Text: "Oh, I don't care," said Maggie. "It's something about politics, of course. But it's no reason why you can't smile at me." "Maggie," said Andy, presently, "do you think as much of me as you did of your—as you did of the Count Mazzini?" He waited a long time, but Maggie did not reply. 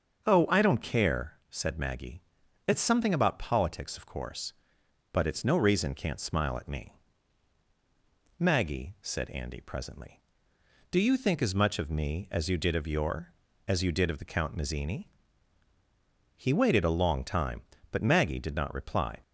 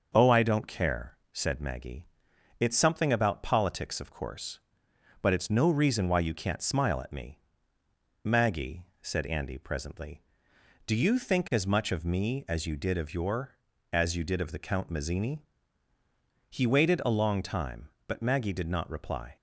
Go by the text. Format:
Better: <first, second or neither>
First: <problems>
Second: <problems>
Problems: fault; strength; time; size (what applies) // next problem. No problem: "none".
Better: second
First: starts louder than the rest; until 1.3 s; 6.5 dB // skips "why you"; at 5.9 s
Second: starts louder than the rest; until 1.1 s; 6.5 dB